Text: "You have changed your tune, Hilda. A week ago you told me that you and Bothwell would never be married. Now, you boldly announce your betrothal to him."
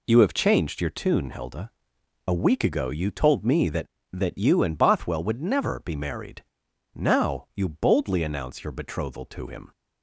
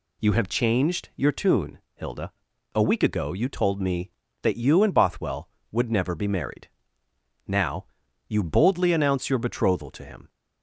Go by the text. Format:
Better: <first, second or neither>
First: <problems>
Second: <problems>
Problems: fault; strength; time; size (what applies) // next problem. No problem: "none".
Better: second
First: says "that" twice; at 4.1 s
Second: none